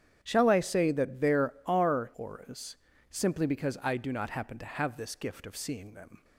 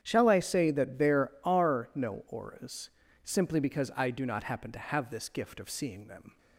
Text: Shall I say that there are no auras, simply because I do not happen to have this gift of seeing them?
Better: second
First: starts louder than the rest; strong; until 1.2 s; 9.5 dB // skips "no"; at 2.1 s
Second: starts louder than the rest; strong; until 1.0 s; 9 dB

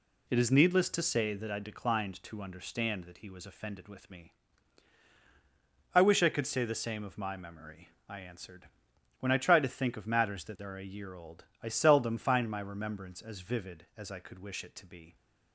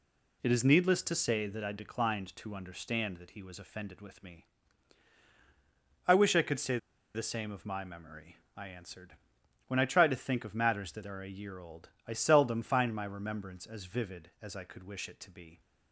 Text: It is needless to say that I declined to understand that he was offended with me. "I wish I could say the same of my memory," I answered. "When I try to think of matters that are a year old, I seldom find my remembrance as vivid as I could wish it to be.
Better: first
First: none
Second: pauses between "say" and "the"; at 6.7 s; 0.37 s long

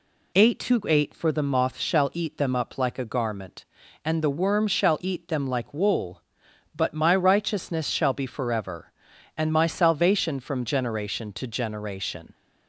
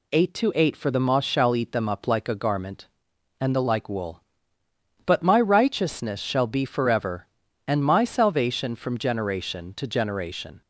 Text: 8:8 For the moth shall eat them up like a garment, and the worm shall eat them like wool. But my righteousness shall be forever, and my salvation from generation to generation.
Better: first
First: none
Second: skips "worm shall eat them"; at 3.6 s

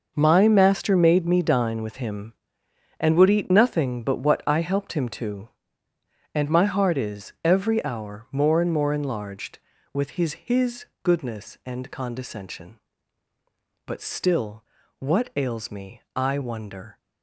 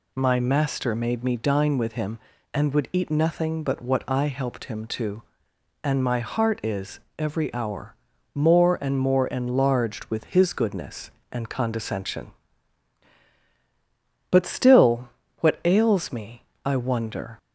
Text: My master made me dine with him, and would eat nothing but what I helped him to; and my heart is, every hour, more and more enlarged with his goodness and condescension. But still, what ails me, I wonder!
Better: second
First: says "his" twice; at 10.3 s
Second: none

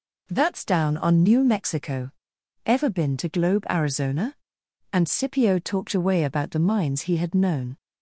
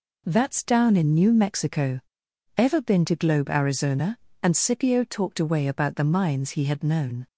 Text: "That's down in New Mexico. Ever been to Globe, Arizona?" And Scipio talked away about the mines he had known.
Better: second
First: says "on" for "in"; at 0.9 s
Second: none

